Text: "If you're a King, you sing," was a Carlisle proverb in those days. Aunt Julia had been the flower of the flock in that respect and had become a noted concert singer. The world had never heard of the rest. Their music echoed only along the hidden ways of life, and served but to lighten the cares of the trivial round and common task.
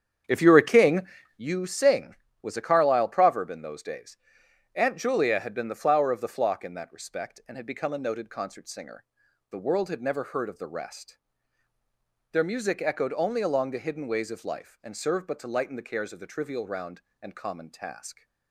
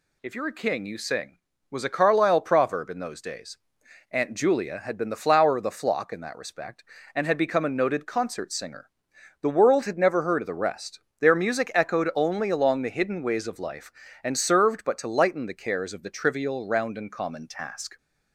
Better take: second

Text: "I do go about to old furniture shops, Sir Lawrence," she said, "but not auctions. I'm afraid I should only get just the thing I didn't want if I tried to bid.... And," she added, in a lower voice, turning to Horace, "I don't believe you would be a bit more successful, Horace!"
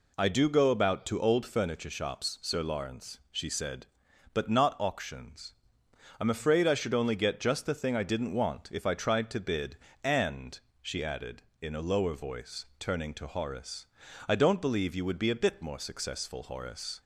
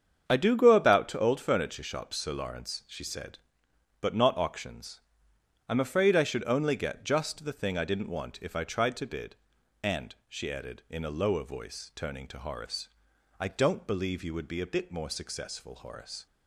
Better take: first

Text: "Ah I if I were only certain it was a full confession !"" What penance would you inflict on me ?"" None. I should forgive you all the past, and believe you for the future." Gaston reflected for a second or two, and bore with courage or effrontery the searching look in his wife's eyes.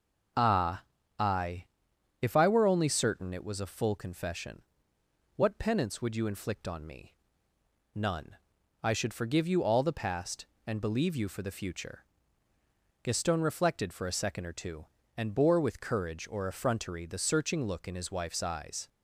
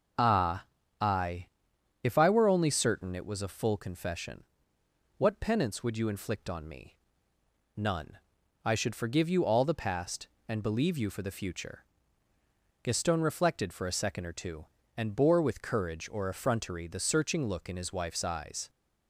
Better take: neither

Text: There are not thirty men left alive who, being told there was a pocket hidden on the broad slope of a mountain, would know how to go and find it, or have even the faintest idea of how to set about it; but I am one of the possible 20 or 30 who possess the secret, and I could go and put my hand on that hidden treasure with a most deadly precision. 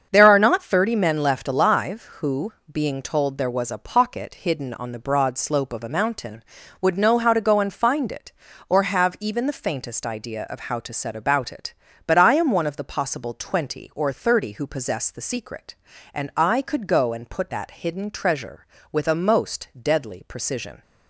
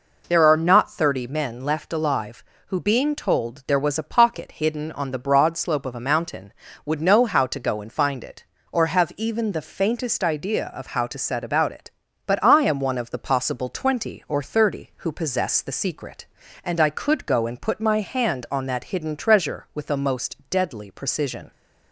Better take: second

